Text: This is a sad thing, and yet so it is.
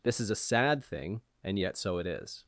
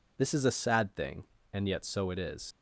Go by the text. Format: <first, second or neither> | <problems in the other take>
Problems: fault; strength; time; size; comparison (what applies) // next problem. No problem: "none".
first | leaves "is" unfinished; at 2.5 s; 75 ms